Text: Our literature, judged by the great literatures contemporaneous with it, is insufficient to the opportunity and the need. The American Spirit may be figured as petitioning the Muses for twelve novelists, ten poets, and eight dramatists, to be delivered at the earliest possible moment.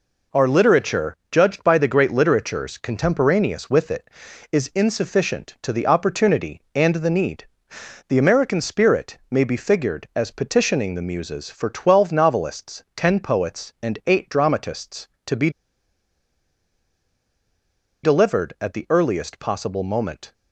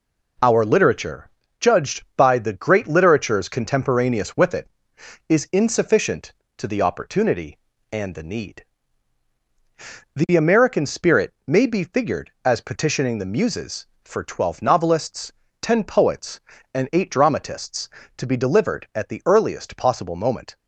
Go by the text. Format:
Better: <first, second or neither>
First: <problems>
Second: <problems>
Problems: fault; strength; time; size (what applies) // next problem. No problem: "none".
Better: second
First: pauses between "be" and "delivered"; strong; at 15.4 s; 2.5 s long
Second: none